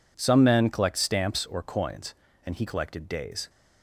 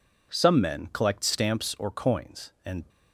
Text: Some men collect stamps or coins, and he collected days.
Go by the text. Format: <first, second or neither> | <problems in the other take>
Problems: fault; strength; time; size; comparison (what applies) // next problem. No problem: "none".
first | stops before "he collected days"; at 2.8 s